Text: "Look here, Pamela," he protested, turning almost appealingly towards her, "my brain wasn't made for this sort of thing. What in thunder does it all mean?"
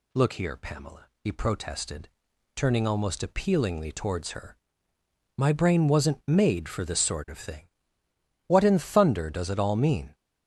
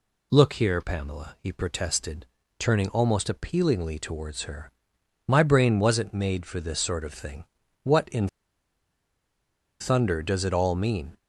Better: first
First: none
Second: pauses between "in" and "thunder"; strong; at 8.2 s; 1.5 s long

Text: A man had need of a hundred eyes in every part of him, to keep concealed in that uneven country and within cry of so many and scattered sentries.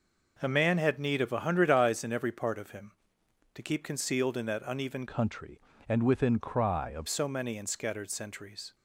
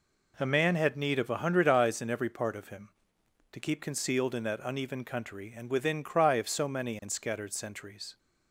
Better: second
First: changes voice from "country" to "of"; from 5.0 to 7.0 s; 2.0 s long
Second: none

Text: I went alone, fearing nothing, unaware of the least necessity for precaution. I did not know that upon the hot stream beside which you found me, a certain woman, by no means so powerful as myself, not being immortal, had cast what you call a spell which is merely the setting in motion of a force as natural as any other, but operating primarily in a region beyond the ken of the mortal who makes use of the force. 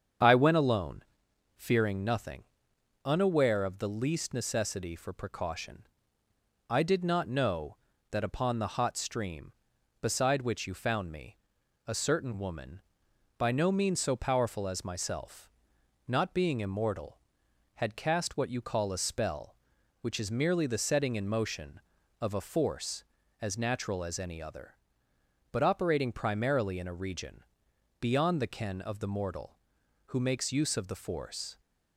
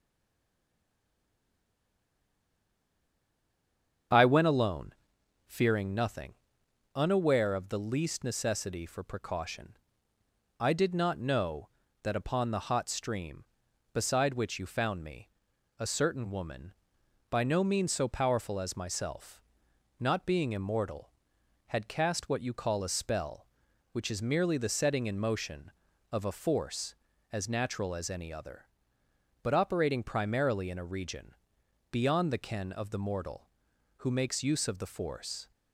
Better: first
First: starts louder than the rest; strong; until 1.7 s; 7.5 dB // pauses between "region" and "beyond"; noticeable; at 27.4 s; 0.60 s long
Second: stays silent before the first word; strong; until 4.1 s; 4.1 s long // starts louder than the rest; strong; until 5.6 s; 7.5 dB // pauses between "region" and "beyond"; noticeable; at 31.3 s; 0.60 s long

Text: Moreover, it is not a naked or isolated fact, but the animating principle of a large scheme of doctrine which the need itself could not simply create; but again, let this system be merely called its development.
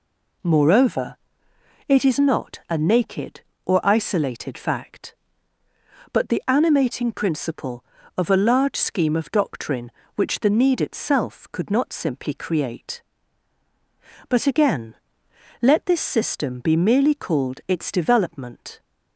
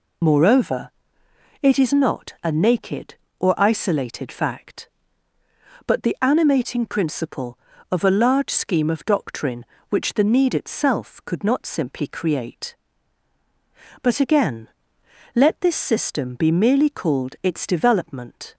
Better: first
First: none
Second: loses the start of "Moreover"; at 0.2 s; 60 ms

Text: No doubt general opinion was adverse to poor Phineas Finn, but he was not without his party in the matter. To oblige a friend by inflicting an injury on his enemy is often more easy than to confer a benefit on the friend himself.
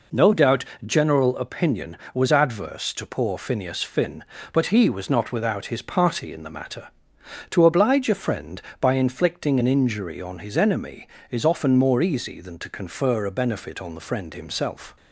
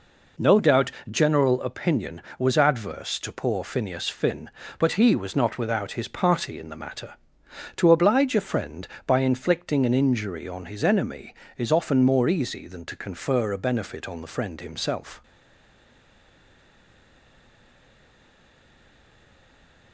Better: first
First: pauses between "doubt" and "general"; slight; at 0.6 s; 0.22 s long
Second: pauses between "doubt" and "general"; slight; at 0.9 s; 0.20 s long // stays silent after the last word; strong; from 15.2 s on; 4.7 s long

